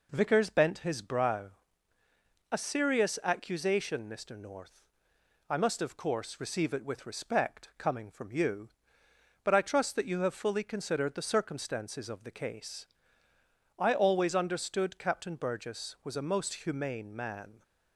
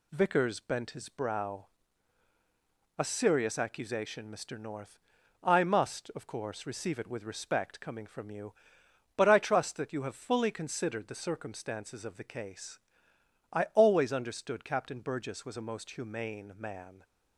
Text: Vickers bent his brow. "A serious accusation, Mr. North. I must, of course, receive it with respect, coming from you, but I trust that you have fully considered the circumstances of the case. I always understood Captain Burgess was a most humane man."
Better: neither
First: none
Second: none

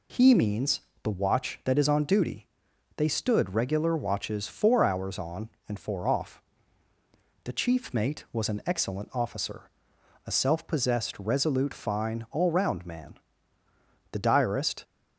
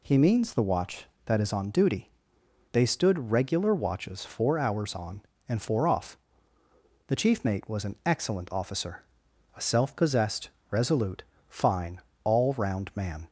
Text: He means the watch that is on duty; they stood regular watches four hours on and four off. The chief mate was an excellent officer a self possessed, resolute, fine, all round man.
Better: second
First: pauses between "means" and "the"; slight; at 0.8 s; 0.22 s long // pauses between "officer" and "a"; noticeable; at 9.6 s; 0.58 s long // goes on to say "The diarist"; noticeable; from 14.1 s on; 0.72 s long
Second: pauses between "officer" and "a"; noticeable; at 9.0 s; 0.52 s long

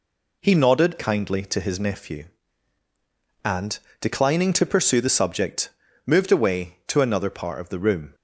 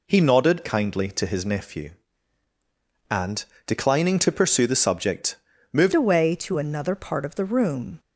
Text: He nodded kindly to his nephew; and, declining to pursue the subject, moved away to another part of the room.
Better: first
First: none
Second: changes voice at "away"; from 5.9 s on; 2.0 s long

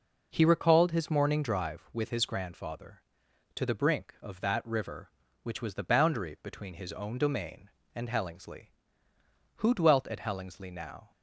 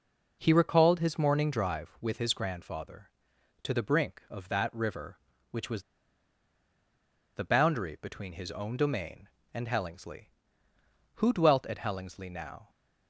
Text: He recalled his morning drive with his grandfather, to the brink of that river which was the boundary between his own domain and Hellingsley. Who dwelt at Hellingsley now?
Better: first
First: none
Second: pauses between "was" and "the"; strong; at 5.8 s; 1.5 s long

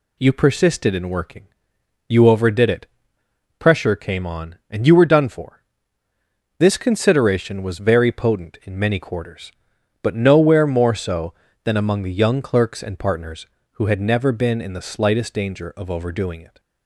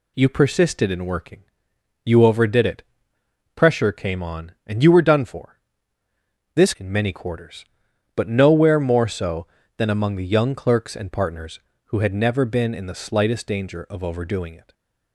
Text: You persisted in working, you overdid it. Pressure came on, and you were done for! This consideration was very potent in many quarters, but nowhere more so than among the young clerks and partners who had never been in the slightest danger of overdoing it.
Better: first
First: none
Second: skips "consideration was very potent"; at 6.7 s

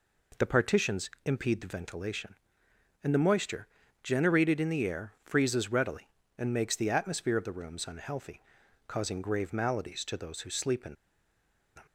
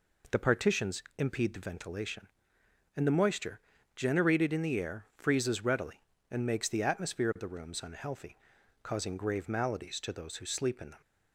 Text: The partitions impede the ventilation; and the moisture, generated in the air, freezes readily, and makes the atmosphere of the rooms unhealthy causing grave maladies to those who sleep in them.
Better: second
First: pauses between "partitions" and "impede"; slight; at 1.0 s; 0.16 s long // pauses between "unhealthy" and "causing"; at 8.4 s; 0.44 s long // pauses between "in" and "them"; noticeable; at 10.9 s; 0.80 s long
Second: pauses between "partitions" and "impede"; slight; at 1.0 s; 0.16 s long // pauses between "unhealthy" and "causing"; at 8.3 s; 0.44 s long

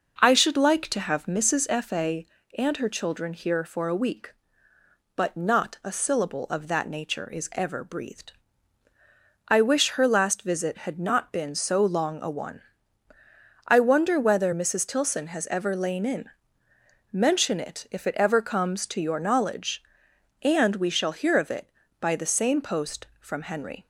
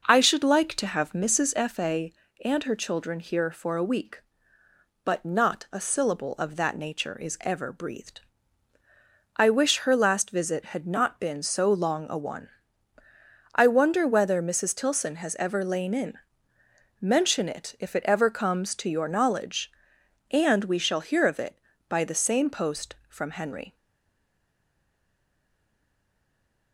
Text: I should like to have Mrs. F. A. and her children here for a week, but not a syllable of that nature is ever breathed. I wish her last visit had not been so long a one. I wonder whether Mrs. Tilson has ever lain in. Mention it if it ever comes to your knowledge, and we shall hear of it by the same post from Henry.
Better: first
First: none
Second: stays silent after the last word; strong; from 23.7 s on; 3.0 s long

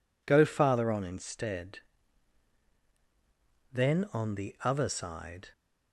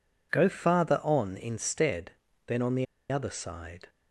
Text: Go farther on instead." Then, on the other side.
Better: first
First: none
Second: pauses between "the" and "other"; slight; at 2.8 s; 0.25 s long

